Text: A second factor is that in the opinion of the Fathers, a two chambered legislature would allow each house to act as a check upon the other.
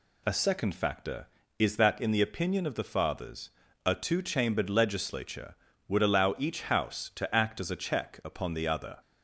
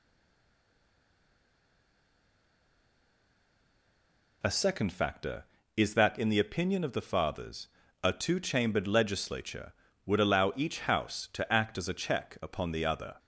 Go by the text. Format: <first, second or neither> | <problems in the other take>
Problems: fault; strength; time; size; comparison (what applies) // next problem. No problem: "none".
first | stays silent before the first word; strong; until 4.4 s; 4.4 s long